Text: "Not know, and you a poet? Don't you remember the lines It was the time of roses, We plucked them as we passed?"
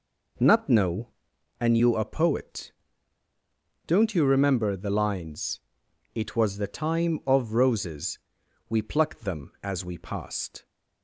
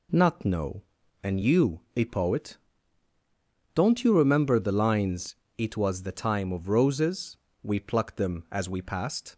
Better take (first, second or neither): second